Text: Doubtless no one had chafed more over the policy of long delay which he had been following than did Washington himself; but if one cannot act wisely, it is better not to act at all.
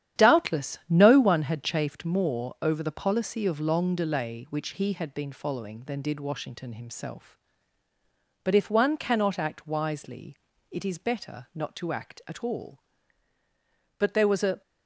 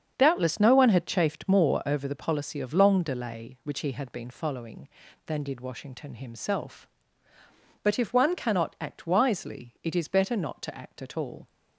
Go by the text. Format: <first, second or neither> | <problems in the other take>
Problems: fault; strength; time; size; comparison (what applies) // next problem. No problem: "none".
second | starts louder than the rest; strong; until 1.2 s; 10 dB; strong in the second // goes on to say "But there was a"; noticeable; from 13.9 s on; 0.62 s long